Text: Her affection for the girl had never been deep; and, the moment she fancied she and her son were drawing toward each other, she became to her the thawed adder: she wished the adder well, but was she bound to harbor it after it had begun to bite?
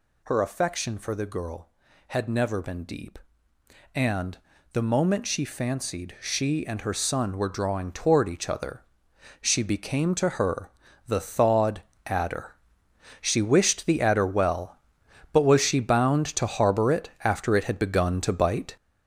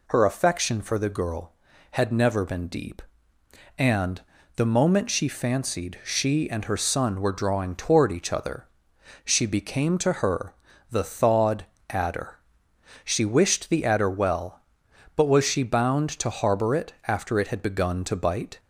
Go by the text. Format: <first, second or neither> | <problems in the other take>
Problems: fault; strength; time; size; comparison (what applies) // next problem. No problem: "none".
second | gets louder; throughout; 7 dB // pauses between "her" and "the"; at 10.6 s; 0.38 s long; also in the second // pauses between "thawed" and "adder"; slight; at 11.8 s; 0.24 s long; slight in the second